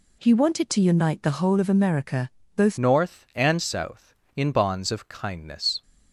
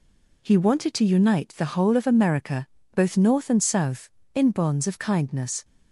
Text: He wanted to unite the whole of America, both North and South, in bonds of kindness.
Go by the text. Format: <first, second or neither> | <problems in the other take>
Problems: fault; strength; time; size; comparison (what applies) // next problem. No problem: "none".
second | changes voice at "North"; from 2.7 s on; 3.1 s long